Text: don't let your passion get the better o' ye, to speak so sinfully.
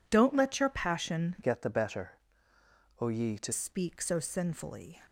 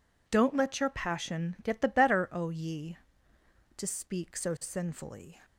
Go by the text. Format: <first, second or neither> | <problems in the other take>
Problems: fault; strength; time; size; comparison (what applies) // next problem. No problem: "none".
second | changes voice from "get" to "to"; from 1.4 to 3.5 s; 2.1 s long // pauses between "better" and "o"; noticeable; at 2.1 s; 0.82 s long